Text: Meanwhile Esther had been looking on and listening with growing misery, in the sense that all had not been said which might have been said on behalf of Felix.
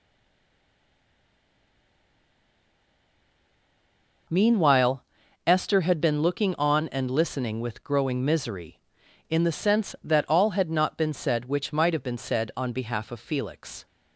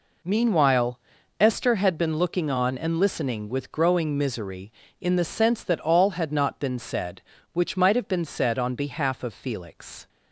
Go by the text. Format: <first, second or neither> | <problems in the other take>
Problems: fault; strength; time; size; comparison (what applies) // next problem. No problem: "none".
second | stays silent before the first word; strong; until 4.2 s; 4.2 s long // pauses between "Meanwhile" and "Esther"; at 5.0 s; 0.42 s long; also in the second